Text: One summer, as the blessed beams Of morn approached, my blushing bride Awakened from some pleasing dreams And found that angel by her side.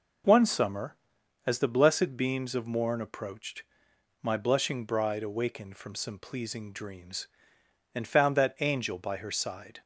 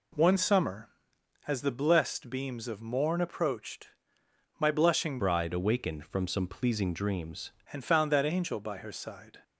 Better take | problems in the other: first | changes voice from "bride" to "dreams"; from 5.1 to 7.5 s; 2.4 s long

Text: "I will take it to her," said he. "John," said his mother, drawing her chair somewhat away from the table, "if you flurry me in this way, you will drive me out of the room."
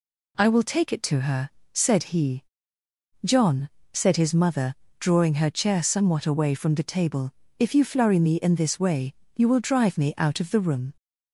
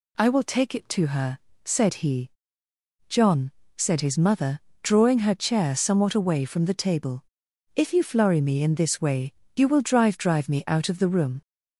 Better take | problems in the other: first | says "drive" twice; at 10.1 s

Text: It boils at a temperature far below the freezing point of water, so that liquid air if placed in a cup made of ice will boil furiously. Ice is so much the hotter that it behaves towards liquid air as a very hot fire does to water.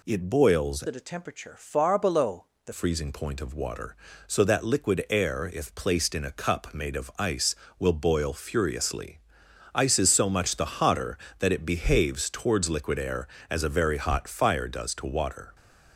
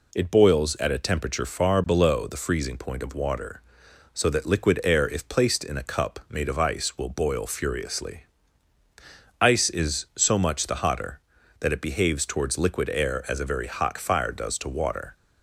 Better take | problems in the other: second | changes voice from "at" to "the"; from 0.8 to 2.7 s; 1.9 s long // pauses between "below" and "the"; slight; at 2.4 s; 0.20 s long

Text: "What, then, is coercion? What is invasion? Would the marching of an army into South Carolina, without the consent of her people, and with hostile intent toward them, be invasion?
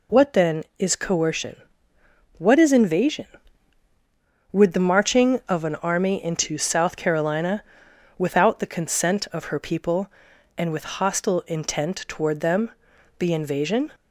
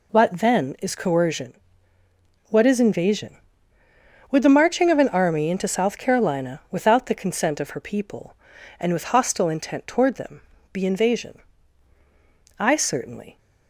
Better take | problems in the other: first | goes on to say "I certainly"; noticeable; from 12.5 s on; 0.80 s long

